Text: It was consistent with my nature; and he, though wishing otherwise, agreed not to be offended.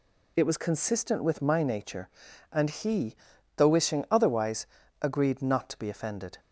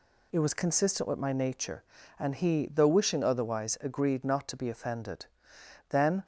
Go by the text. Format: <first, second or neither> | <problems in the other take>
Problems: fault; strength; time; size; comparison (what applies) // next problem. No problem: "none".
first | goes on to say "Then"; slight; from 5.9 s on; 0.34 s long